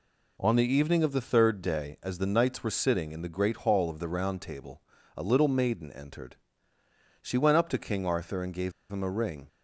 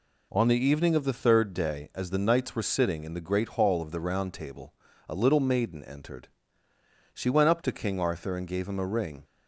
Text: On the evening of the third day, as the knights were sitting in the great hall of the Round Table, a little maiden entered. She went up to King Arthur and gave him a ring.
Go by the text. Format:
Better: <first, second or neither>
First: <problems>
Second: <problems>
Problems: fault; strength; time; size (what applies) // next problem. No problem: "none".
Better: second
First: pauses between "gave" and "him"; slight; at 8.7 s; 0.20 s long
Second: none